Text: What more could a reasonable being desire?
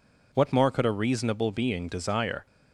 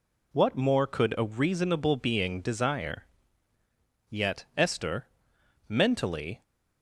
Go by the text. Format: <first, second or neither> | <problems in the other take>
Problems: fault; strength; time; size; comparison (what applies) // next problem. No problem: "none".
first | goes on to say "Yet Esther mentally"; strong; from 4.0 s on; 2.3 s long